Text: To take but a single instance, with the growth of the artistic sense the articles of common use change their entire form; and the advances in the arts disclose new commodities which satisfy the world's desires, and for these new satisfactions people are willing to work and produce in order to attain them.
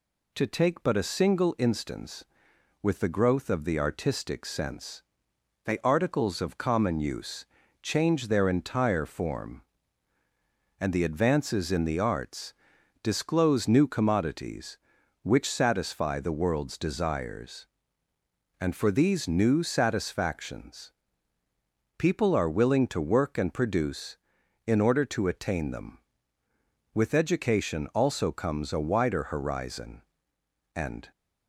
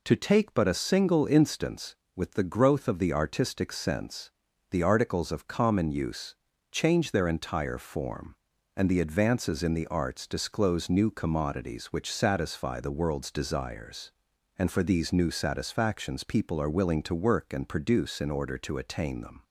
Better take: second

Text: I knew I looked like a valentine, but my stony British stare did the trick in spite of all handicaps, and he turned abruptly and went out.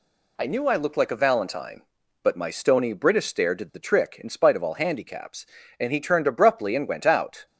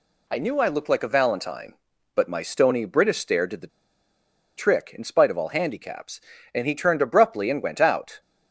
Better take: first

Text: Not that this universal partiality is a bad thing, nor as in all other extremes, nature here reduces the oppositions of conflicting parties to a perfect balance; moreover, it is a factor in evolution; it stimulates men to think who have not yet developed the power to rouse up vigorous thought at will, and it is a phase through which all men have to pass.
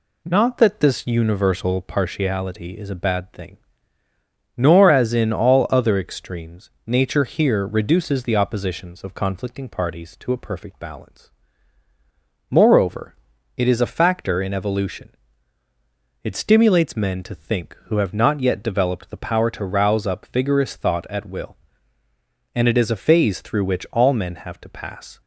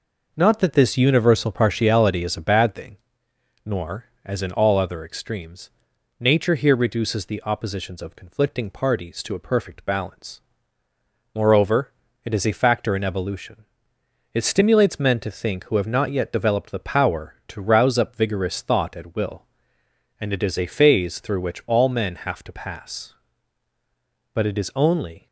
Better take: first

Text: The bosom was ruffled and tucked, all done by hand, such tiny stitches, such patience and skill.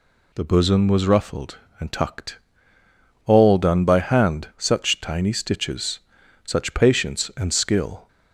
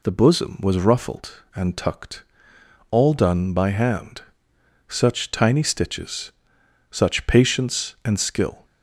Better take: neither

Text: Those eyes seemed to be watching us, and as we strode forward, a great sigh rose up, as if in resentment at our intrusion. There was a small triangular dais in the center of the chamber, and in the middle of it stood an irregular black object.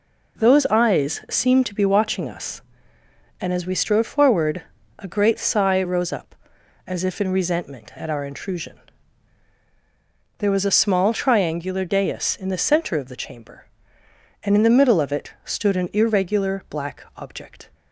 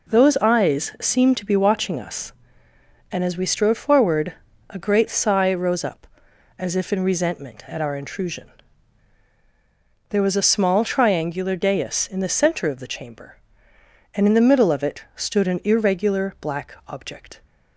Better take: neither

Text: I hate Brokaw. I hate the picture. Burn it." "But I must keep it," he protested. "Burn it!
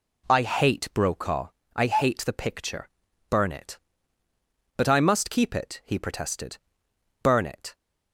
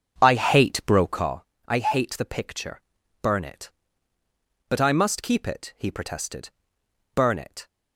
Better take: first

